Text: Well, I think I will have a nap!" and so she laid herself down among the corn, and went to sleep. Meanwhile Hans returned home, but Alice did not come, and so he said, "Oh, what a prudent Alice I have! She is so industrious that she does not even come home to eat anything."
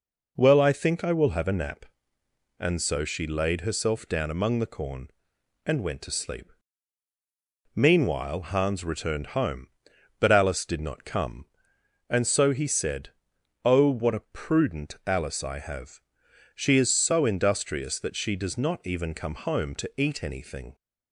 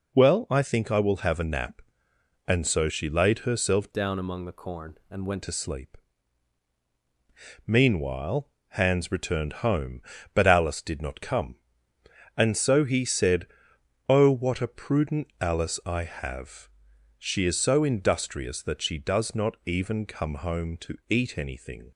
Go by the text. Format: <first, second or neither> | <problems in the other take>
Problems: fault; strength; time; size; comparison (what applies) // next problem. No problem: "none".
first | changes voice from "down" to "went"; from 3.9 to 5.4 s; 1.5 s long // pauses between "Meanwhile" and "Hans"; slight; at 8.4 s; 0.20 s long